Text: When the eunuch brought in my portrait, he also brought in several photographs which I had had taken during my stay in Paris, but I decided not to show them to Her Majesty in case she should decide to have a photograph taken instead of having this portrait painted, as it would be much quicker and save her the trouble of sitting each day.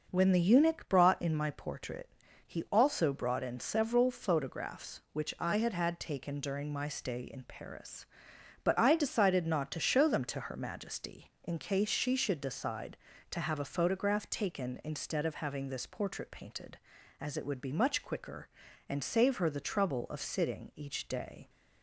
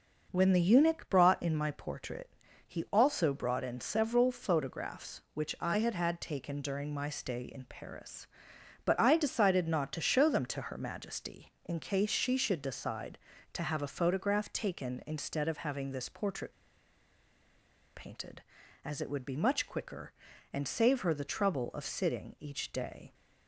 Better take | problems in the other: first | pauses between "portrait" and "painted"; strong; at 16.5 s; 1.4 s long

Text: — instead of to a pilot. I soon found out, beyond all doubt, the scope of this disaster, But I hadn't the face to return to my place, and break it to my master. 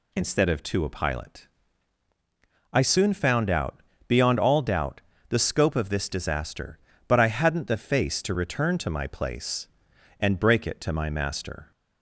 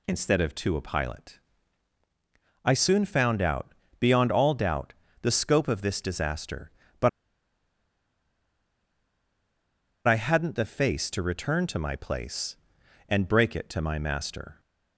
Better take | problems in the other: first | pauses between "But" and "I"; strong; at 7.0 s; 2.9 s long

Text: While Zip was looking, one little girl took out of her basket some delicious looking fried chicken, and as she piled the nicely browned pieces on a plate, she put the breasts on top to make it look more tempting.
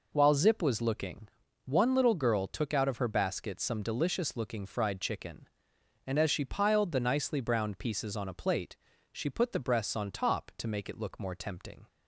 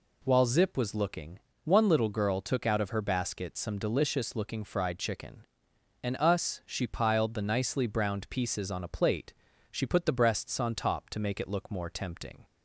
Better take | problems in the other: first | says "us" for "as"; at 6.1 s

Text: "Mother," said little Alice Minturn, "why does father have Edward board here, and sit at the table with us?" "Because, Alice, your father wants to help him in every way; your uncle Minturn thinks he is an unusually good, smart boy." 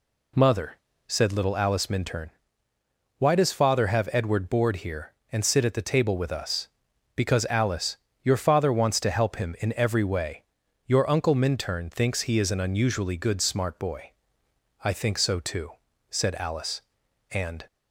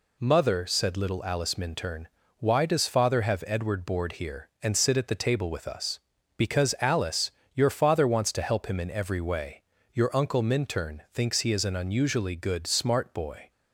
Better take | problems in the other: second | goes on to say "I think so too said Alice and"; strong; from 14.8 s on; 2.8 s long

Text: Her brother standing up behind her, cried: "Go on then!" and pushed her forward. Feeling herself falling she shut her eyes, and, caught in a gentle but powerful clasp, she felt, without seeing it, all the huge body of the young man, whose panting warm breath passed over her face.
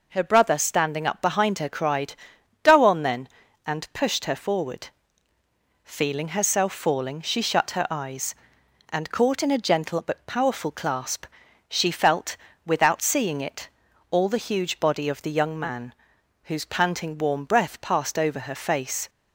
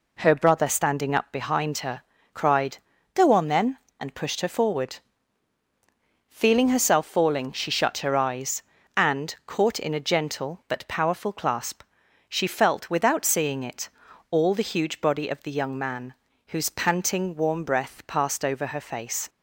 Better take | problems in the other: neither | none

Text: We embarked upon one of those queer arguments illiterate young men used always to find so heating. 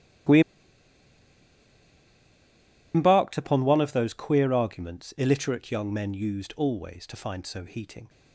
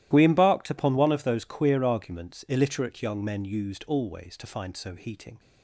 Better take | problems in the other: second | starts louder than the rest; strong; until 3.8 s; 14.5 dB; strong in the second // pauses between "We" and "embarked"; strong; at 0.4 s; 2.5 s long

